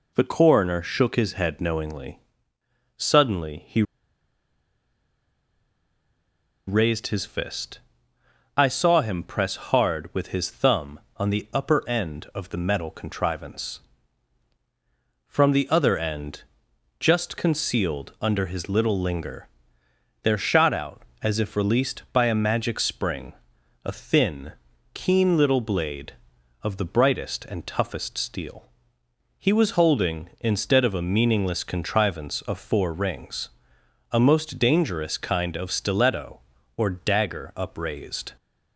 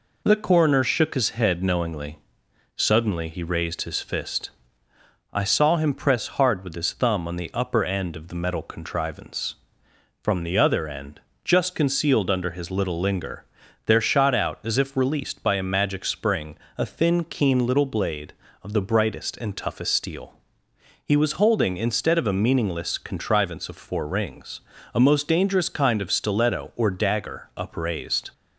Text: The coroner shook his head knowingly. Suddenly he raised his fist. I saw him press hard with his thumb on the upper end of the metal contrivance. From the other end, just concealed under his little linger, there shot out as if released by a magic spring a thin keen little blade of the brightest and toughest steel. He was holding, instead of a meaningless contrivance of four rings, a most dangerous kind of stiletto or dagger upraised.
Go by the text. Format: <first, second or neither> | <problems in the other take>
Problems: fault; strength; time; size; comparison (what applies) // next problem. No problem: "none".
second | pauses between "he" and "raised"; strong; at 3.8 s; 2.8 s long // pauses between "spring" and "a"; noticeable; at 23.3 s; 0.50 s long; slight in the second // pauses between "thin" and "keen"; at 24.5 s; 0.40 s long